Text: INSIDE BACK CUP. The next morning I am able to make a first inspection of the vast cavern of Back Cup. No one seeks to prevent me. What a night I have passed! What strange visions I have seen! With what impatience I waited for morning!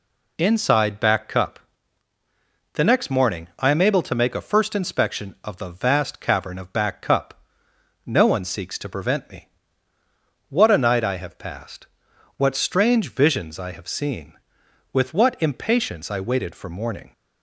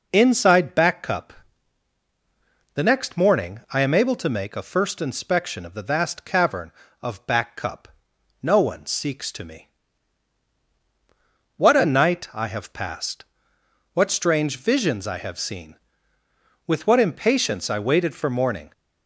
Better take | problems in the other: first | skips "prevent"; at 9.4 s

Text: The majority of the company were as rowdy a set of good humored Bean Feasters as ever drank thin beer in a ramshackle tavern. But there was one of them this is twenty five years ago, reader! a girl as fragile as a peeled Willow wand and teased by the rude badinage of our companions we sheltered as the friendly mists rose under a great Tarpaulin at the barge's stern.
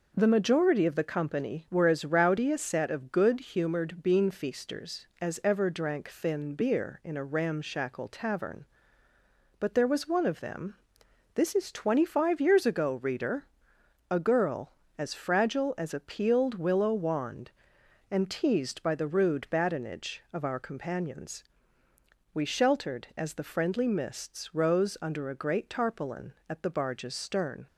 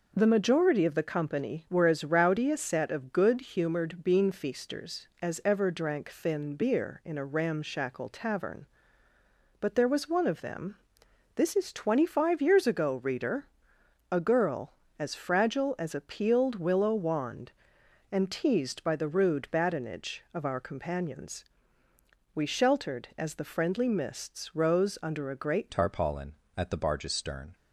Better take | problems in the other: first | pauses between "them" and "this"; noticeable; at 10.7 s; 0.60 s long; noticeable in the first // pauses between "companions" and "we"; noticeable; at 21.4 s; 0.92 s long; noticeable in the first // changes voice at "Tarpaulin"; from 25.7 s on; 1.8 s long

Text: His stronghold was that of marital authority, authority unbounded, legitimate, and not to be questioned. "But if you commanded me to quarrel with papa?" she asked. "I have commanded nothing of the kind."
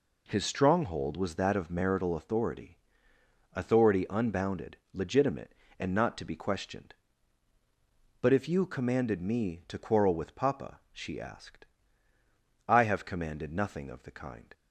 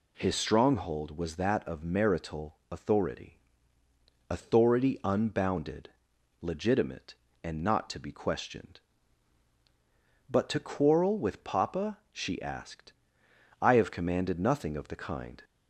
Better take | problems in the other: first | pauses between "marital" and "authority"; slight; at 2.5 s; 0.16 s long // skips "if you commanded me"; at 10.4 s

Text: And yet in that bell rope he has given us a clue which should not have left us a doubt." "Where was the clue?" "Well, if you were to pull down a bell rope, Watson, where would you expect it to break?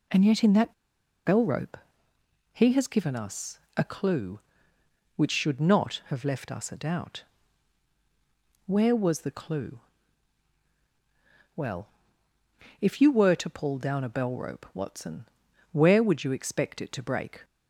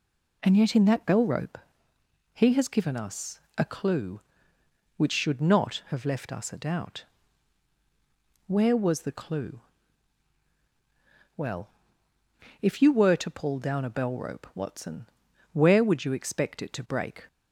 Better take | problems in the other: second | pauses between "that" and "bell"; noticeable; at 0.7 s; 0.51 s long // pauses between "rope" and "he"; noticeable; at 1.7 s; 0.76 s long; noticeable in the second // pauses between "us" and "a"; slight; at 3.5 s; 0.16 s long; slight in the second

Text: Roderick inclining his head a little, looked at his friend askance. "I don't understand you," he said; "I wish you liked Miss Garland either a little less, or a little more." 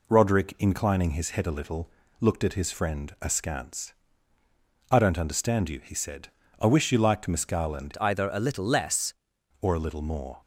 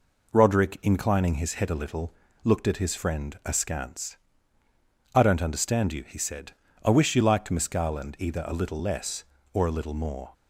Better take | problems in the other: second | changes voice from "either" to "less"; from 7.9 to 9.1 s; 1.2 s long

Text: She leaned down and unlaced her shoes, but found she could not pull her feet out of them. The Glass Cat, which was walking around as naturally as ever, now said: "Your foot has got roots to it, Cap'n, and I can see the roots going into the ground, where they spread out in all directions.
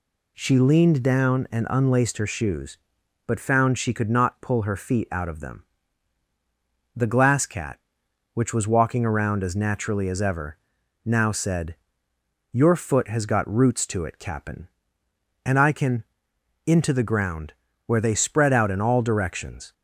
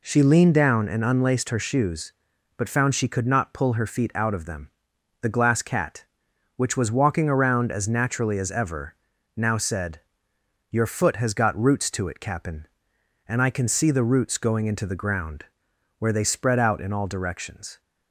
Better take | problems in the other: second | skips "see the roots going"; at 16.3 s

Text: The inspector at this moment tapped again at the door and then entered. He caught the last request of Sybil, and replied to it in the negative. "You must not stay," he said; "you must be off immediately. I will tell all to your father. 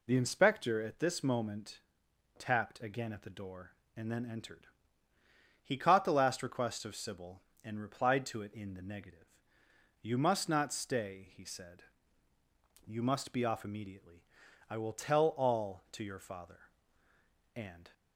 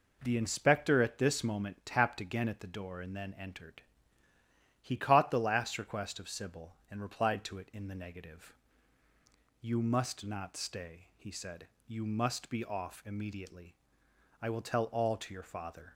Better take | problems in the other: second | pauses between "moment" and "tapped"; noticeable; at 1.7 s; 0.58 s long // goes on to say "And"; slight; from 17.5 s on; 0.38 s long

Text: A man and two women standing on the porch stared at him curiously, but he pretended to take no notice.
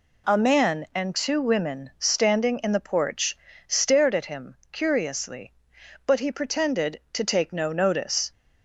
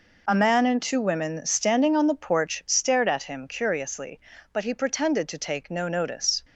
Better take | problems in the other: second | says "in" for "on"; at 2.6 s // pauses between "porch" and "stared"; slight; at 3.3 s; 0.30 s long

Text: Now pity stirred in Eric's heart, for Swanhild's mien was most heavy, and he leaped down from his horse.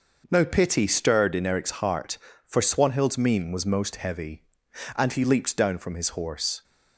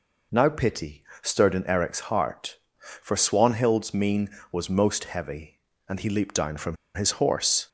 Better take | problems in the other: first | pauses between "pity" and "stirred"; slight; at 1.0 s; 0.20 s long // pauses between "from" and "his"; slight; at 6.7 s; 0.19 s long

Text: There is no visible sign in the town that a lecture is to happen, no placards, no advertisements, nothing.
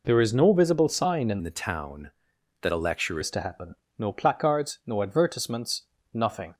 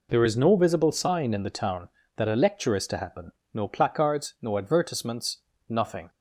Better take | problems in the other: second | changes voice from "the" to "lecture"; from 1.4 to 3.1 s; 1.7 s long

